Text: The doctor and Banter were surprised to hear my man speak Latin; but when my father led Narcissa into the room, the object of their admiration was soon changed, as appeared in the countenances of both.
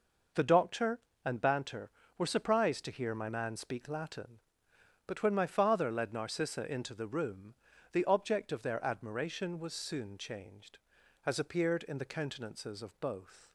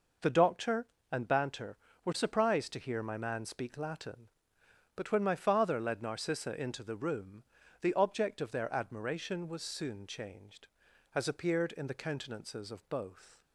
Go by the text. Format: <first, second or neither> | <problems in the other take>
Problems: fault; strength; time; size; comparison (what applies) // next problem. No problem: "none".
neither | none